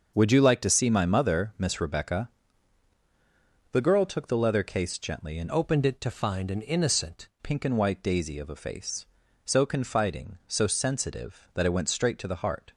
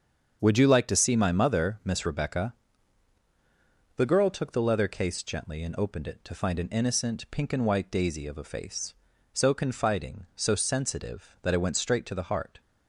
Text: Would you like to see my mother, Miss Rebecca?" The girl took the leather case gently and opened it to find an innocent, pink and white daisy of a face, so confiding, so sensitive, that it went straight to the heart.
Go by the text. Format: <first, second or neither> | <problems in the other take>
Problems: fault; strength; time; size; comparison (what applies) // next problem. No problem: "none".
second | starts louder than the rest; until 1.1 s; 6.5 dB; strong in the second // changes voice from "opened" to "innocent"; from 5.5 to 7.2 s; 1.7 s long